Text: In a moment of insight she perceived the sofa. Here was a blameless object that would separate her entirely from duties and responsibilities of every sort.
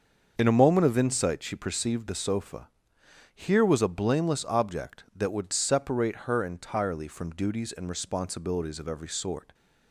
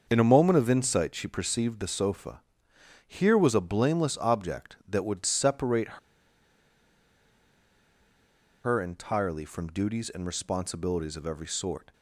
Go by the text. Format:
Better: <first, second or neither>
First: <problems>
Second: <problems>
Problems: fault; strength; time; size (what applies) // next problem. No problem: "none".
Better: first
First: starts louder than the rest; until 1.3 s; 6.5 dB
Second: starts louder than the rest; until 1.1 s; 6.5 dB // pauses between "separate" and "her"; strong; at 5.9 s; 2.6 s long